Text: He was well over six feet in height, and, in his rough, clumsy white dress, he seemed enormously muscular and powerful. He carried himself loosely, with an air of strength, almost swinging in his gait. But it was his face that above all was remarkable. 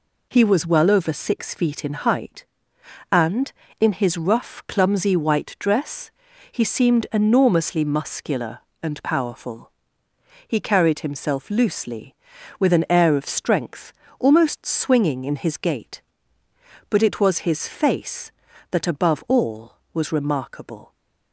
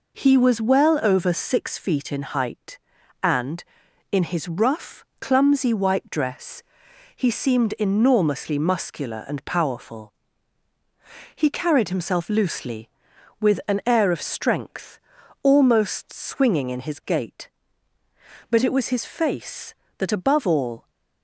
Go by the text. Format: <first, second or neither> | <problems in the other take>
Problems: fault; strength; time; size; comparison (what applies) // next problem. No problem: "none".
first | stops before "was remarkable"; at 20.8 s